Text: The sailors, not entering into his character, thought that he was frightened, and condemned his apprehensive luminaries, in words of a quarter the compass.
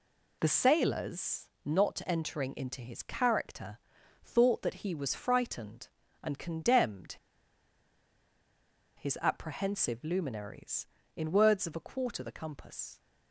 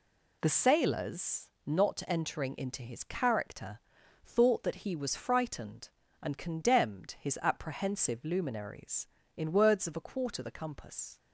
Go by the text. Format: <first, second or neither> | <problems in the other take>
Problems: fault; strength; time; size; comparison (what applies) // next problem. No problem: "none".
second | pauses between "condemned" and "his"; strong; at 7.1 s; 1.8 s long